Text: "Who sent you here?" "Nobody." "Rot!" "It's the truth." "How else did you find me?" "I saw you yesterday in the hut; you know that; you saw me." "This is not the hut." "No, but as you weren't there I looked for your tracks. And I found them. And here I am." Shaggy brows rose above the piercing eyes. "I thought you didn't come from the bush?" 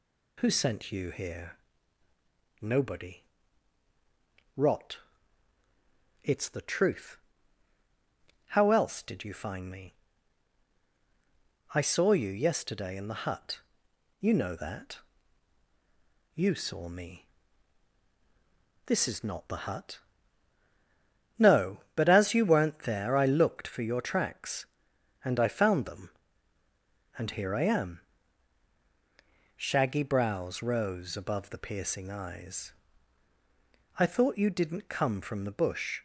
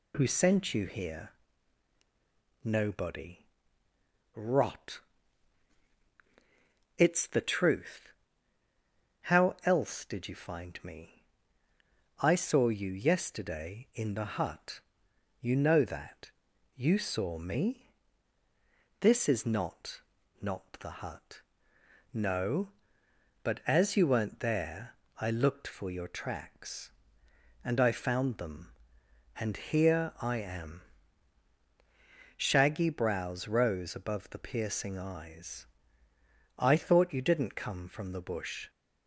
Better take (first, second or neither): first